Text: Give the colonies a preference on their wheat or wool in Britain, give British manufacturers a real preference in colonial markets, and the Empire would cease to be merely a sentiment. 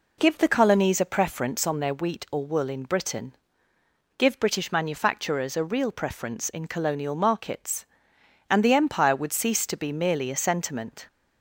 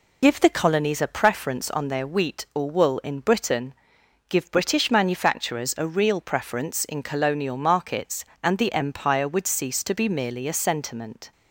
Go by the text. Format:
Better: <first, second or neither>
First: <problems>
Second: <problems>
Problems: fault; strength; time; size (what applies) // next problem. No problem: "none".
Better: first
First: none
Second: loses the start of "Give"; at 0.2 s; 55 ms